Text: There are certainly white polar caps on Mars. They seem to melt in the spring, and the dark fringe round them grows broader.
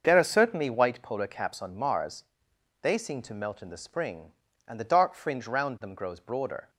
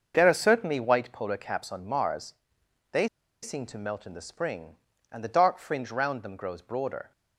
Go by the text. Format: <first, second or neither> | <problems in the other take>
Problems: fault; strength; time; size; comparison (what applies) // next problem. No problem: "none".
first | starts louder than the rest; until 1.1 s; 6.5 dB; also in the first // pauses between "They" and "seem"; at 3.0 s; 0.36 s long